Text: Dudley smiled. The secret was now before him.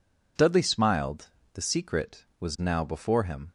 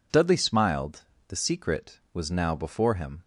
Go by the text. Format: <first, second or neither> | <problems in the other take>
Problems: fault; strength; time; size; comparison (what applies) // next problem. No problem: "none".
neither | none